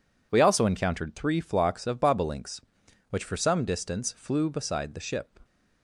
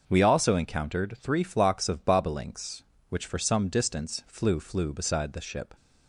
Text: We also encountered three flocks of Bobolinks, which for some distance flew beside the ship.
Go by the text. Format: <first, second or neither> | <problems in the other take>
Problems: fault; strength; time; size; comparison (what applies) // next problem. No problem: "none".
first | starts louder than the rest; until 1.0 s; 6.5 dB // says "flew" twice; at 4.5 s